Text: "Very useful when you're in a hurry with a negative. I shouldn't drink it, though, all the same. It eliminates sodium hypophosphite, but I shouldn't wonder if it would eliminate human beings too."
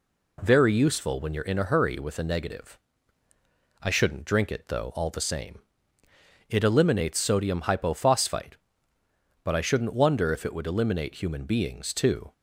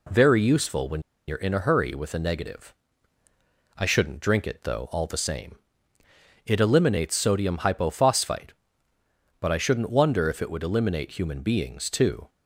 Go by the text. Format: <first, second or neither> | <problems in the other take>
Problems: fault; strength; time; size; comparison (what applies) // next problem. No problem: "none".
first | pauses between "when" and "you're"; slight; at 1.0 s; 0.26 s long